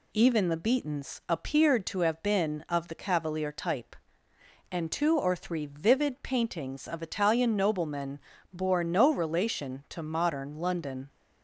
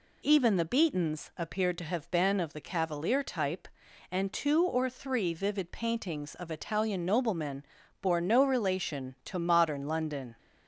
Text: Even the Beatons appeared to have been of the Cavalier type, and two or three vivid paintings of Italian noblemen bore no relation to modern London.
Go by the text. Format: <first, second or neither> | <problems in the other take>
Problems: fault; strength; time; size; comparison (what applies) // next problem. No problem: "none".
neither | pauses between "noblemen" and "bore"; slight; the same in both